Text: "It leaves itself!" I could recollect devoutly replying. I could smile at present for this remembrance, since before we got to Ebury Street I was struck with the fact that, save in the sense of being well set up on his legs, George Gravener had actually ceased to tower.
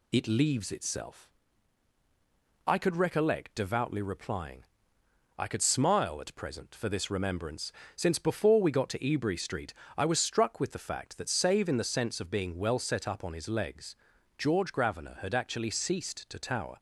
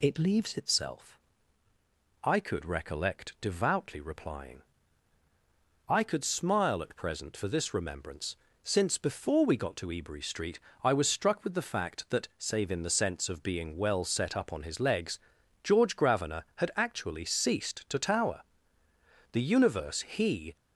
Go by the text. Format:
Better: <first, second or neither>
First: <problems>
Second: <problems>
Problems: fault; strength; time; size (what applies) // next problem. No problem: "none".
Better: first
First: pauses between "Street" and "I"; slight; at 9.7 s; 0.24 s long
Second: pauses between "Street" and "I"; slight; at 10.5 s; 0.24 s long // goes on to say "The universe he"; noticeable; from 19.3 s on; 1.2 s long